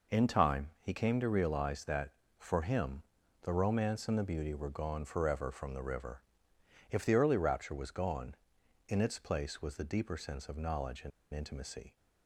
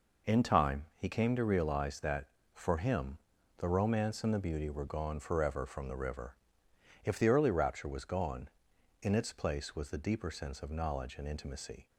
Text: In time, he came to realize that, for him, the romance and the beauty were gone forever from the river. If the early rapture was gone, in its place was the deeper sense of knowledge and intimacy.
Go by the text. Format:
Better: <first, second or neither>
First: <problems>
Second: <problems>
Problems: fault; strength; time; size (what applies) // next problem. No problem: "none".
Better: second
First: pauses between "and" and "intimacy"; slight; at 11.1 s; 0.23 s long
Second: none